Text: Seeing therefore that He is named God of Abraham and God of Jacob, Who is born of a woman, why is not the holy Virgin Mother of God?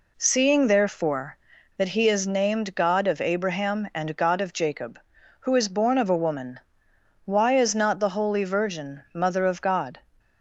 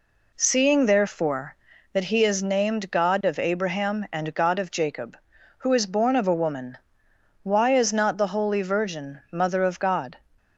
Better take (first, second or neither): neither